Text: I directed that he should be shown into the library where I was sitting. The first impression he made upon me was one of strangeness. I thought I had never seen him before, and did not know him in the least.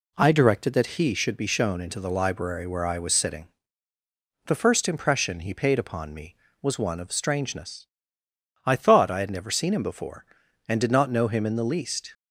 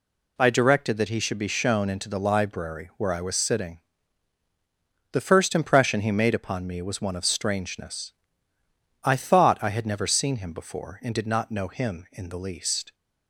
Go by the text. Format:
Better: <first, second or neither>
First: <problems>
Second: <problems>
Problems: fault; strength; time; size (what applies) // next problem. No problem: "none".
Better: second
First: says "paid" for "made"; at 5.5 s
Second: none